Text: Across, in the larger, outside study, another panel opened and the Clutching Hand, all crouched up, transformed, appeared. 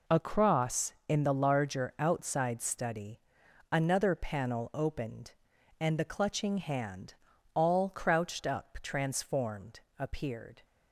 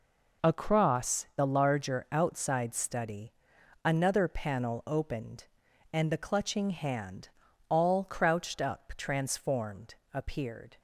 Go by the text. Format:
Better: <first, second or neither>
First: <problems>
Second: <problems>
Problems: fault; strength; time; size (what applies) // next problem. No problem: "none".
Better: first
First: none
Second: skips "in"; at 1.3 s